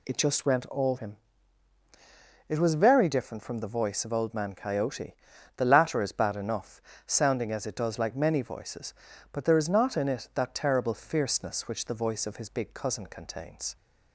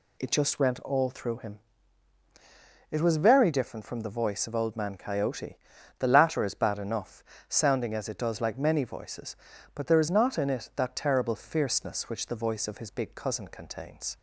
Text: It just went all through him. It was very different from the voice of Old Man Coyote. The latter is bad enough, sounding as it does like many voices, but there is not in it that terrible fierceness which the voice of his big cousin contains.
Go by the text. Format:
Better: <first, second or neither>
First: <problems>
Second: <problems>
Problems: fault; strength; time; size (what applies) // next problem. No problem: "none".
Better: second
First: skips "through"; at 0.9 s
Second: none